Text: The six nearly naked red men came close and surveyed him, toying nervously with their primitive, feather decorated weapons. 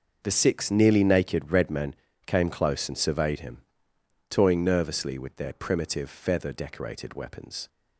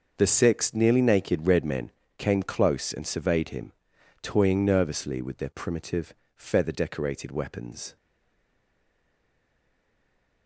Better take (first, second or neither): first